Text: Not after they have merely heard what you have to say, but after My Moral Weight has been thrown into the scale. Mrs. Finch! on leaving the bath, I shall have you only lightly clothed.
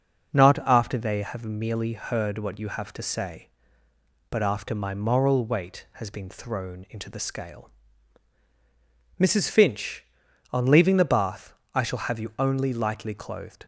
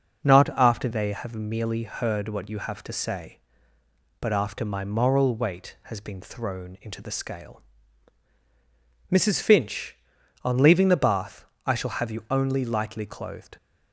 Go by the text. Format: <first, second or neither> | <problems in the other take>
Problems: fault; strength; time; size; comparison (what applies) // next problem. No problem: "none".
neither | none